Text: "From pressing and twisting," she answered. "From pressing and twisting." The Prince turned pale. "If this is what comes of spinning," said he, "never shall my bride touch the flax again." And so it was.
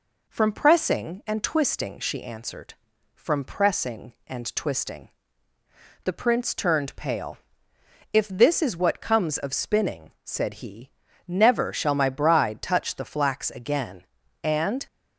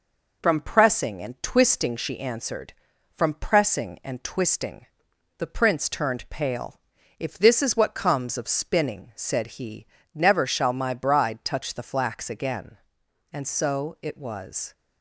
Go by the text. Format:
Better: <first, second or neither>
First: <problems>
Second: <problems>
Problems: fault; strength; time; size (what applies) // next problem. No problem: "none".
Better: second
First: stops before "so it was"; at 14.8 s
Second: none